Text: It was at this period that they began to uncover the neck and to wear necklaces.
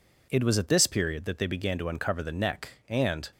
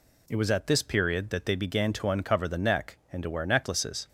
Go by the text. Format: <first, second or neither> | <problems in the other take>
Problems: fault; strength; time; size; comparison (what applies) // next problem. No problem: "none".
second | stops before "to wear necklaces"; at 3.3 s